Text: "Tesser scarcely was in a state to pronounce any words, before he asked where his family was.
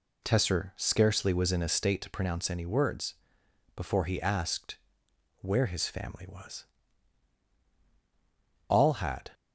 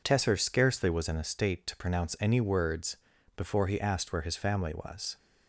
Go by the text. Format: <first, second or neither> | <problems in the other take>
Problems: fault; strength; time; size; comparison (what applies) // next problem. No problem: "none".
second | pauses between "asked" and "where"; noticeable; at 4.7 s; 0.64 s long // goes on to say "All had"; noticeable; from 8.6 s on; 0.62 s long